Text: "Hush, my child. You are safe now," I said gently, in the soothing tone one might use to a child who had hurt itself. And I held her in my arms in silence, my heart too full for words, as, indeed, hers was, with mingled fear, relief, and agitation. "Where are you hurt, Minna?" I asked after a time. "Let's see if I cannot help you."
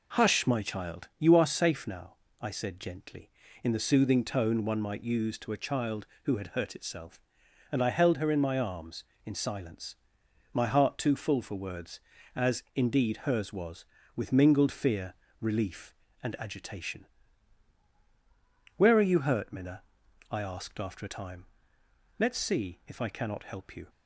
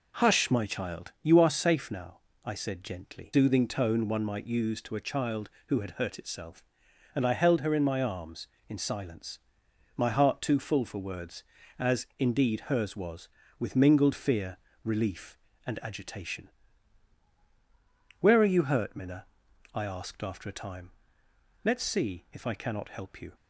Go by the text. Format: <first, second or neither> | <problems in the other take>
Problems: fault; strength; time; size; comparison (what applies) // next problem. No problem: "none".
first | skips "in the"; at 3.3 s